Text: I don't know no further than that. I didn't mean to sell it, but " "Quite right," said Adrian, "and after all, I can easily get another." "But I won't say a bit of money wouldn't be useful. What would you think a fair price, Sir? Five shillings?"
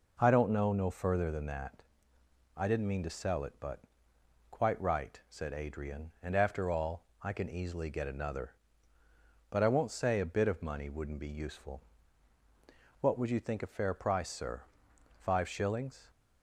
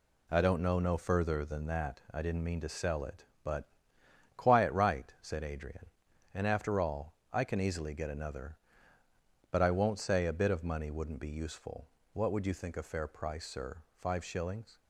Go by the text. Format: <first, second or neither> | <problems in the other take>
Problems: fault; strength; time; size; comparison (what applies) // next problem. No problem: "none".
first | says "Quiet" for "Quite"; at 4.3 s